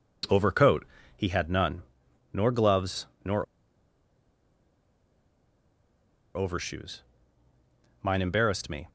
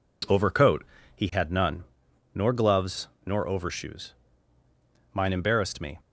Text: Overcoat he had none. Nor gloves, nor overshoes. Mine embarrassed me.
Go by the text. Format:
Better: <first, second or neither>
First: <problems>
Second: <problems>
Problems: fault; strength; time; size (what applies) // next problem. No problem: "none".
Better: second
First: pauses between "Overcoat" and "he"; slight; at 0.8 s; 0.30 s long // pauses between "nor" and "overshoes"; strong; at 3.4 s; 2.9 s long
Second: pauses between "Overcoat" and "he"; slight; at 0.8 s; 0.30 s long